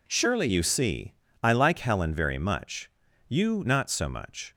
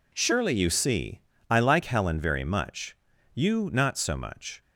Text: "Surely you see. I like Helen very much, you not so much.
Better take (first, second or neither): neither